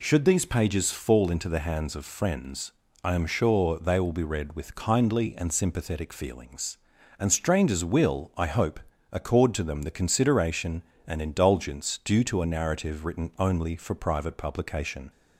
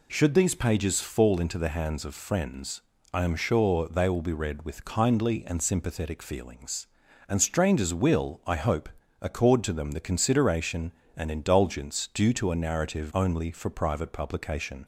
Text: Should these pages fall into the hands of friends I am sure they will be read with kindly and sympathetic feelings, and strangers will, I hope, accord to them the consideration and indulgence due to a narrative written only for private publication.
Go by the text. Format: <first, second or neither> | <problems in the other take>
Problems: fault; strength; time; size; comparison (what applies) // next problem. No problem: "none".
first | pauses between "friends" and "I"; slight; at 2.8 s; 0.32 s long; slight in the first // skips "written"; at 13.1 s